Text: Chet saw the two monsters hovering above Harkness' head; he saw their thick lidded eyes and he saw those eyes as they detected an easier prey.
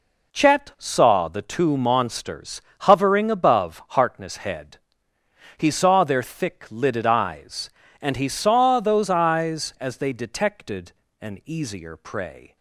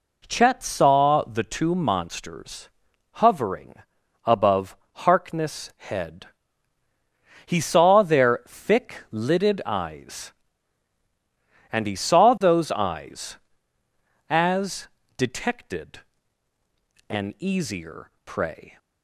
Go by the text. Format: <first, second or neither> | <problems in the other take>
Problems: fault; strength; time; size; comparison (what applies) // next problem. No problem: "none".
first | pauses between "monsters" and "hovering"; at 2.6 s; 0.44 s long; slight in the first // pauses between "hovering" and "above"; noticeable; at 3.7 s; 0.52 s long // pauses between "above" and "Harkness"; slight; at 4.7 s; 0.22 s long // skips "they"; at 15.0 s // pauses between "detected" and "an"; at 15.9 s; 1.0 s long; slight in the first